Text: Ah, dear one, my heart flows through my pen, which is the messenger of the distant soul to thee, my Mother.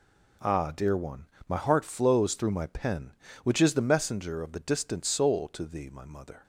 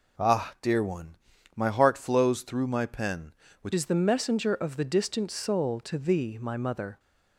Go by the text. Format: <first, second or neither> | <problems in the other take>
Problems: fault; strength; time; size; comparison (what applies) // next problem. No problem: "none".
first | changes voice at "is"; from 3.7 s on; 3.2 s long